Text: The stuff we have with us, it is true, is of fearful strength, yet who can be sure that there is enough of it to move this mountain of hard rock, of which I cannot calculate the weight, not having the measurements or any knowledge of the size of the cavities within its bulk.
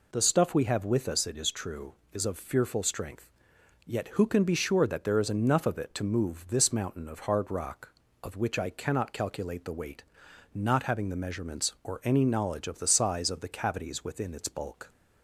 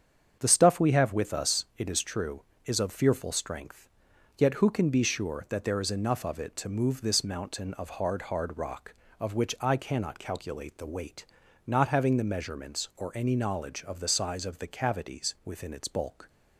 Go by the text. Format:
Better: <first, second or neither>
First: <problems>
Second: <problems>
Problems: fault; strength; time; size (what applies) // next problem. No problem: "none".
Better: first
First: none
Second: starts louder than the rest; strong; until 1.4 s; 7.5 dB // says "hard" twice; at 8.2 s